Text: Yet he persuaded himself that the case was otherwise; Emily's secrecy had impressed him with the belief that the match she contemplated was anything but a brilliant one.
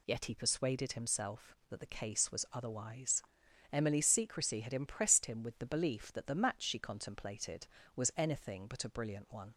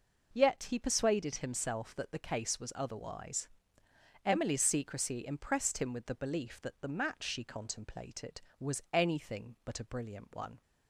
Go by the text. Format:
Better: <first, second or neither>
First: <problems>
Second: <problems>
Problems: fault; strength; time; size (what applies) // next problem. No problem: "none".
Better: first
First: none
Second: skips "had"; at 5.2 s